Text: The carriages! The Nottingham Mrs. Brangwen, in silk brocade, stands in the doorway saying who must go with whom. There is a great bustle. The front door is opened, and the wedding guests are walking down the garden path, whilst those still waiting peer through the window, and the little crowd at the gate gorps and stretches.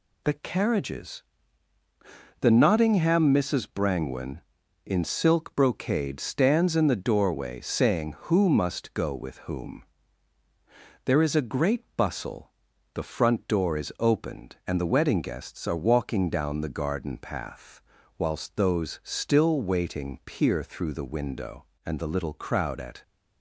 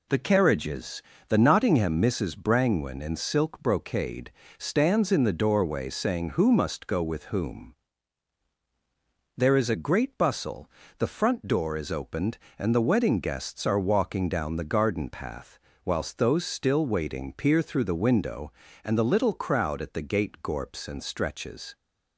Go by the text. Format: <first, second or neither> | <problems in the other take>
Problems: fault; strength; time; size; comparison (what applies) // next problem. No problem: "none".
second | stops before "the gate gorps and stretches"; at 23.0 s